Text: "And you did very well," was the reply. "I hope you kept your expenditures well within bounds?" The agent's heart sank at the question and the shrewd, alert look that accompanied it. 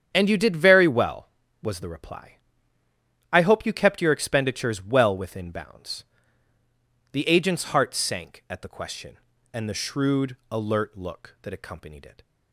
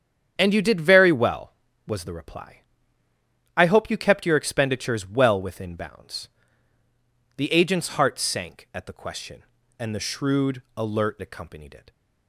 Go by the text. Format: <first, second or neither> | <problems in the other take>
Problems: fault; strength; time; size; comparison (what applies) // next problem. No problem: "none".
first | starts louder than the rest; strong; until 1.3 s; 8.5 dB; strong in the first // skips "look that"; at 11.2 s